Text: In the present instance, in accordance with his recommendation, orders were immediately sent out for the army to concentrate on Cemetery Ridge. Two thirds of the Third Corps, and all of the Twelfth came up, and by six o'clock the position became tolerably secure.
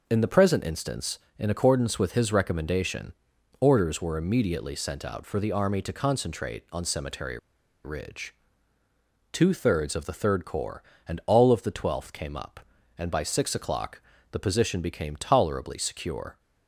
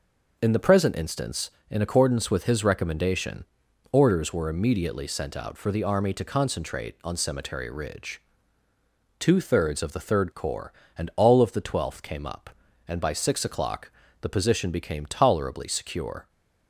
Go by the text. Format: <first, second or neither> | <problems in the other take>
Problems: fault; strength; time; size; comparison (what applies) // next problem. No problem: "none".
second | pauses between "Cemetery" and "Ridge"; at 7.3 s; 0.44 s long // pauses between "o'clock" and "the"; slight; at 14.0 s; 0.32 s long; slight in the second